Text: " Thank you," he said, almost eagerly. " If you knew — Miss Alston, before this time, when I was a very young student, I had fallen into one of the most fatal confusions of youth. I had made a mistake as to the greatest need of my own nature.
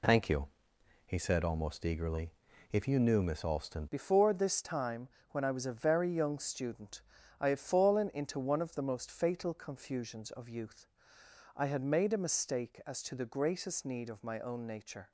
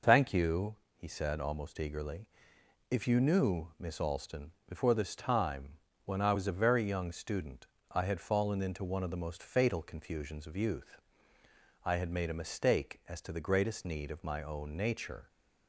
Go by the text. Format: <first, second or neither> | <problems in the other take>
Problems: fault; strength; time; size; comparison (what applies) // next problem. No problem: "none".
second | changes voice at "before"; from 3.9 s on; 11.2 s long